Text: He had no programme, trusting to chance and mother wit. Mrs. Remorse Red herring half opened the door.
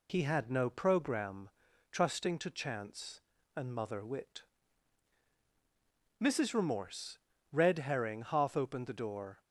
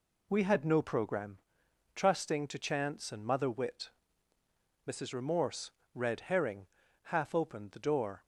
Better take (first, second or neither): first